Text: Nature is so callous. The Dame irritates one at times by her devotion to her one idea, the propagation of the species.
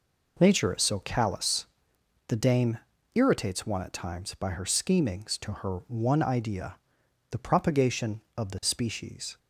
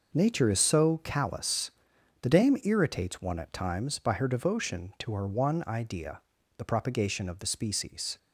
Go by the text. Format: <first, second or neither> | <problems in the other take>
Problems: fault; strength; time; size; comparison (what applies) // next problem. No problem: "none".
second | pauses between "Dame" and "irritates"; at 2.7 s; 0.38 s long // says "schemings" for "devotion"; at 4.6 s